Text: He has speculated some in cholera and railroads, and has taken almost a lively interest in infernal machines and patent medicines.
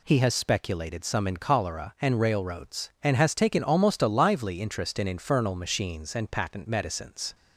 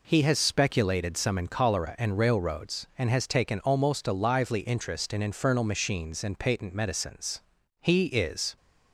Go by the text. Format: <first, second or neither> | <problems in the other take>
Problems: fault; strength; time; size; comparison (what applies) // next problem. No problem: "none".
first | goes on to say "He is"; noticeable; from 7.8 s on; 0.74 s long